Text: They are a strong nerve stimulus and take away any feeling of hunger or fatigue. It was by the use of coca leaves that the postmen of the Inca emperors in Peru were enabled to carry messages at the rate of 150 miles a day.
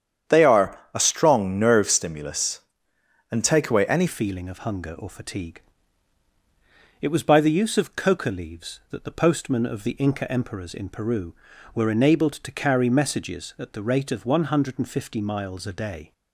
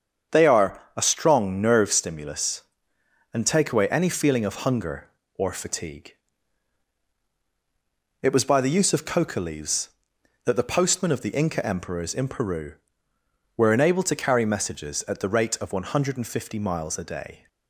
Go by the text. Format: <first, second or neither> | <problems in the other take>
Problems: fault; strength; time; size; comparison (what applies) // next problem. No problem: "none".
second | starts louder than the rest; strong; until 1.4 s; 9 dB; strong in the second // pauses between "are" and "a"; slight; at 0.7 s; 0.16 s long; slight in the second // changes voice at "feeling"; from 4.0 s on; 12.1 s long